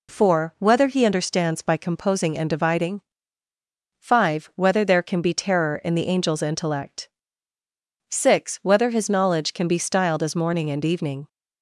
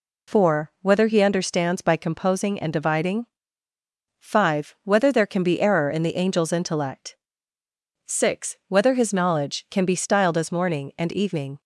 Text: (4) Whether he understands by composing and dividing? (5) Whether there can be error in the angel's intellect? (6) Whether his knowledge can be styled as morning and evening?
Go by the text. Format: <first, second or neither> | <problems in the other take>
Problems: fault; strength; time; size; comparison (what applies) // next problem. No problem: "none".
second | says "terror" for "error"; at 5.3 s